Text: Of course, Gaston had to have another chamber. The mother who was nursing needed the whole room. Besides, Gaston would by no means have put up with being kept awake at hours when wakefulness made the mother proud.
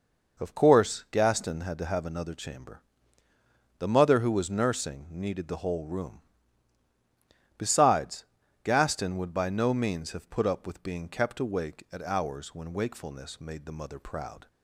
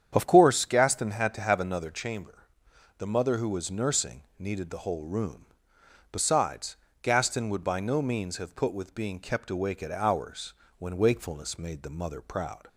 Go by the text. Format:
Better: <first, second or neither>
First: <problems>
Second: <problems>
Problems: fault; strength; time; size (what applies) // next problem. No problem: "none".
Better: first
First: none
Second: starts louder than the rest; strong; until 1.1 s; 8.5 dB // pauses between "nursing" and "needed"; slight; at 4.2 s; 0.16 s long // skips "up"; at 8.7 s // pauses between "hours" and "when"; slight; at 10.5 s; 0.24 s long